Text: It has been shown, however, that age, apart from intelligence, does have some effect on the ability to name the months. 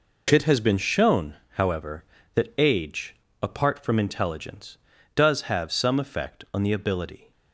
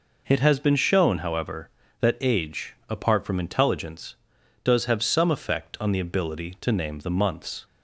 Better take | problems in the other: second | stops before "to name the months"; at 7.3 s

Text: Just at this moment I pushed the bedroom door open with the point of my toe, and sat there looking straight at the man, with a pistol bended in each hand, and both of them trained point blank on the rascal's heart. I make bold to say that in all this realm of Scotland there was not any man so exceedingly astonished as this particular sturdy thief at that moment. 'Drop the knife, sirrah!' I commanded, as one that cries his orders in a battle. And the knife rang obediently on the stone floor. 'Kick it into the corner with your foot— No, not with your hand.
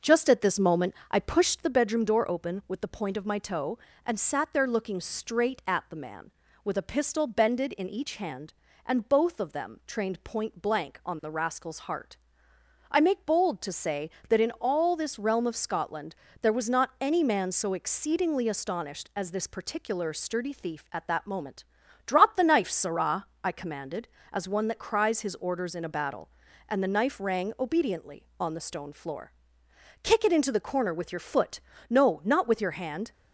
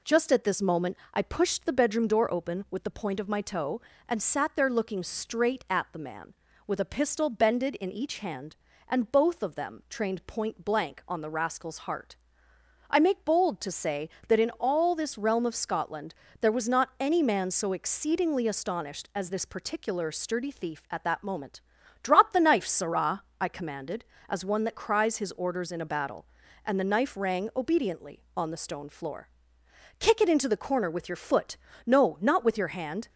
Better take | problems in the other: second | starts louder than the rest; noticeable; until 1.7 s; 6 dB // pauses between "moment" and "I"; slight; at 0.9 s; 0.16 s long; slight in the second // pauses between "Scotland" and "there"; slight; at 16.1 s; 0.28 s long; slight in the second

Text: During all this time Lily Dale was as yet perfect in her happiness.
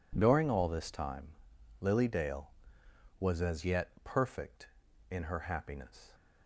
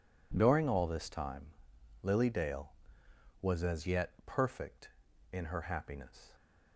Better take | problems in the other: neither | pauses between "time" and "Lily"; noticeable; the same in both

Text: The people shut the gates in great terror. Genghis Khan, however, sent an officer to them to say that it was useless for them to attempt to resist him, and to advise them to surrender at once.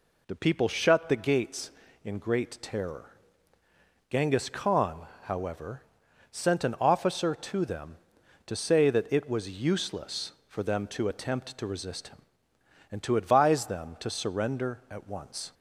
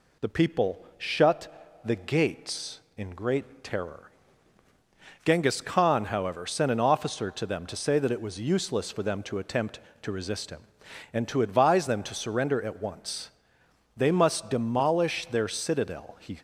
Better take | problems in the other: first | goes on to say "They must demolish their citadel he"; strong; from 13.9 s on; 2.4 s long

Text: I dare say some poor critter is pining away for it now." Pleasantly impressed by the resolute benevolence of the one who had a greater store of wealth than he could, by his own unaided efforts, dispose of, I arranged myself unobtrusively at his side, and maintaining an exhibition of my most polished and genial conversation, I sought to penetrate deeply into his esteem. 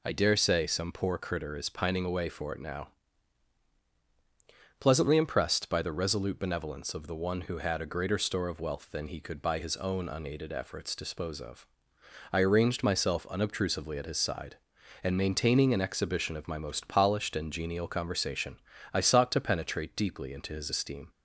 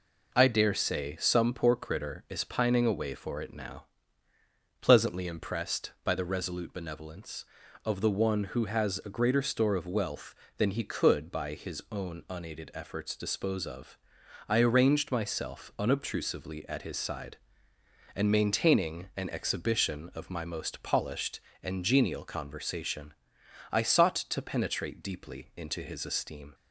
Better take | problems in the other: first | says "has" for "had"; at 8.6 s

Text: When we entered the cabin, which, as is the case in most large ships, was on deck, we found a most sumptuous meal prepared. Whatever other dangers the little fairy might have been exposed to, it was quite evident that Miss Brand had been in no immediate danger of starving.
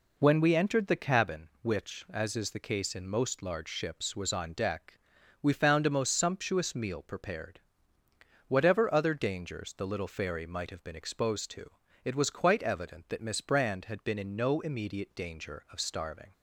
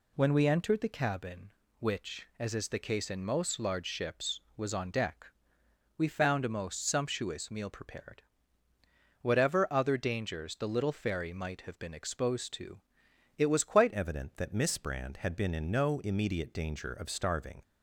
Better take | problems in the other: first | changes voice at "evident"; from 13.9 s on; 3.7 s long

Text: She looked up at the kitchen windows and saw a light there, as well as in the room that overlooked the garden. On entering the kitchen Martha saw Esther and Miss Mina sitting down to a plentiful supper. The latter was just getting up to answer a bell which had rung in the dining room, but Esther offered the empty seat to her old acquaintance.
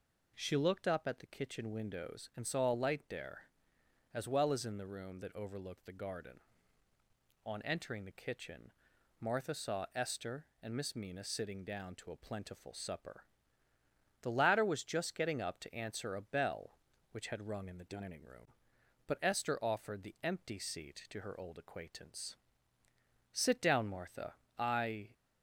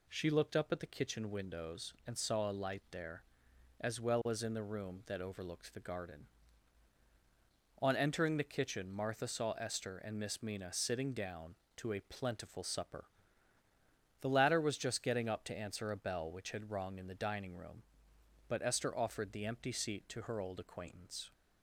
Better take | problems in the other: second | pauses between "kitchen" and "Martha"; noticeable; at 8.7 s; 0.50 s long // goes on to say "Sit down Martha I"; strong; from 23.3 s on; 1.7 s long

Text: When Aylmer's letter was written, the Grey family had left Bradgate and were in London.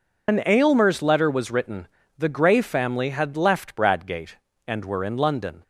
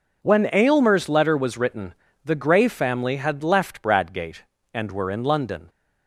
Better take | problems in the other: second | loses the start of "When"; at 0.2 s; 120 ms

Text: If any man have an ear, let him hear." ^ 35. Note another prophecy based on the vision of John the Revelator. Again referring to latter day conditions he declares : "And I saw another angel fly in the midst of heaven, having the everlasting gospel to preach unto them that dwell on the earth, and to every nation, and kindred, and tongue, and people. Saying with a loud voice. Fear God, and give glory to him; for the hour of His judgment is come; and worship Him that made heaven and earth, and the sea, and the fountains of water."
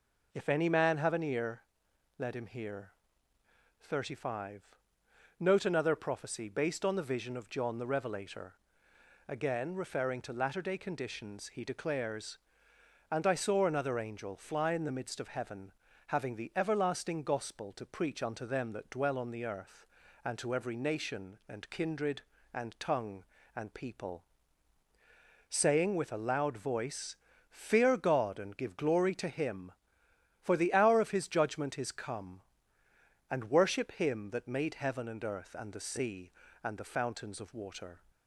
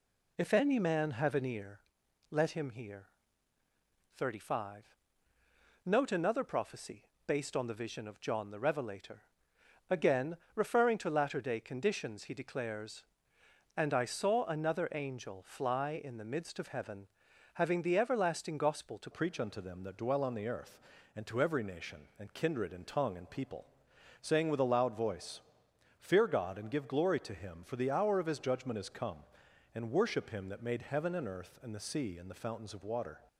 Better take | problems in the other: first | pauses between "prophecy" and "based"; slight; at 7.0 s; 0.20 s long // pauses between "Again" and "referring"; slight; at 10.3 s; 0.18 s long // changes voice at "preach"; from 19.1 s on; 14.1 s long

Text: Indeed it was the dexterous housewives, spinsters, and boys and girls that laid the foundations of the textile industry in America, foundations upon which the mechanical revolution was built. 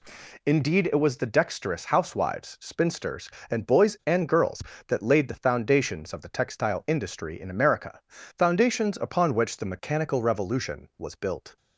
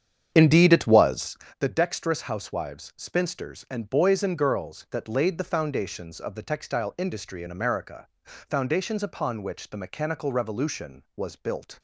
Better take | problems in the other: first | starts louder than the rest; strong; until 1.4 s; 8.5 dB // pauses between "was" and "the"; slight; at 1.3 s; 0.22 s long

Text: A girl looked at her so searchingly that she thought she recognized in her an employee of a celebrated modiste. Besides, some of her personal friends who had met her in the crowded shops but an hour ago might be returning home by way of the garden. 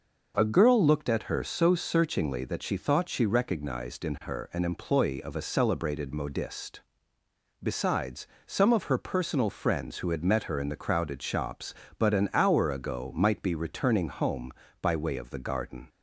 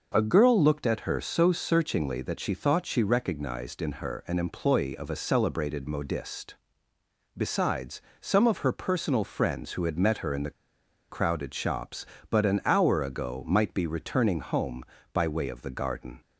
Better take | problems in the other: first | pauses between "the" and "crowded"; noticeable; at 10.5 s; 0.59 s long

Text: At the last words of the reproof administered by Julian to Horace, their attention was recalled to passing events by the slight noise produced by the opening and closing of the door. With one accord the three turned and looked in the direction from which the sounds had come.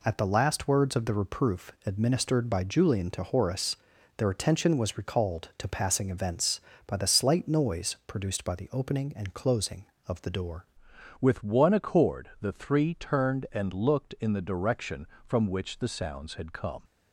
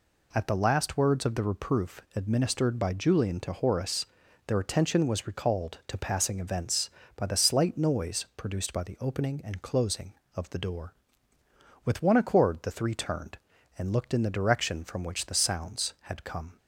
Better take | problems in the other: second | changes voice at "With"; from 11.1 s on; 5.7 s long

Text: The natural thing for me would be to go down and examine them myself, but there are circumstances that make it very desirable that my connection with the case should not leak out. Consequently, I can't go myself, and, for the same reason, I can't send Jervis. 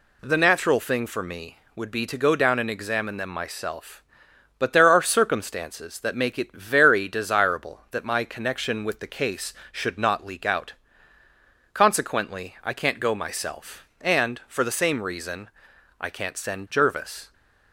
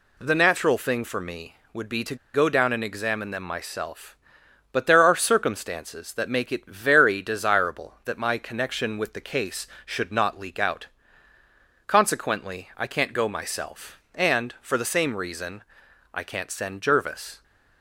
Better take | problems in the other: first | pauses between "to" and "go"; slight; at 2.1 s; 0.18 s long

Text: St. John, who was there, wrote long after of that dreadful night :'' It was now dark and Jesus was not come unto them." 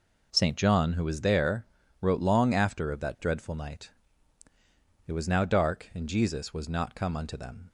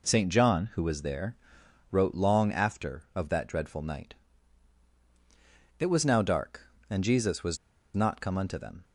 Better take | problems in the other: first | pauses between "was" and "not"; at 7.5 s; 0.38 s long

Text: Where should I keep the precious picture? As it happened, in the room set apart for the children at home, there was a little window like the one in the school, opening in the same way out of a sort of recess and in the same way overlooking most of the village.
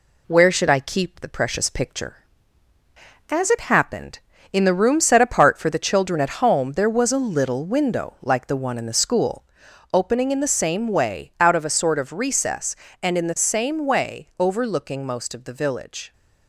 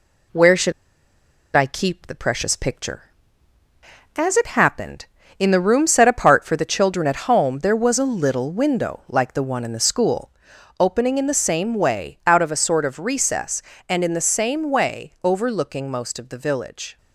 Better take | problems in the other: first | pauses between "should" and "I"; noticeable; at 0.7 s; 0.84 s long

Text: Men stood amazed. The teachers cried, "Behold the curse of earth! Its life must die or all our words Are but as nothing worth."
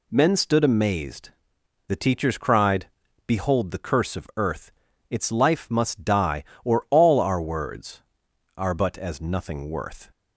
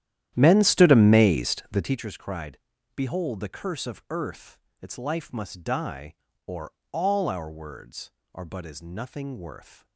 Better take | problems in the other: first | starts louder than the rest; strong; until 2.0 s; 11.5 dB // pauses between "or" and "all"; slight; at 6.7 s; 0.22 s long

